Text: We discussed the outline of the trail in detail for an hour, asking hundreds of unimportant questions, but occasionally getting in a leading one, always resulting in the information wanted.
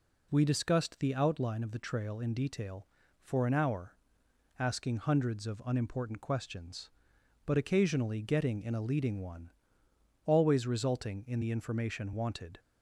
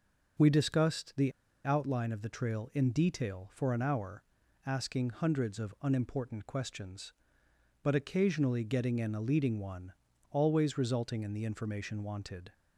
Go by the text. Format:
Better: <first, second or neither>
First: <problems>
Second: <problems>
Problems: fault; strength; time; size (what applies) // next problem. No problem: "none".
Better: first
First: none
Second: pauses between "the" and "outline"; slight; at 1.3 s; 0.32 s long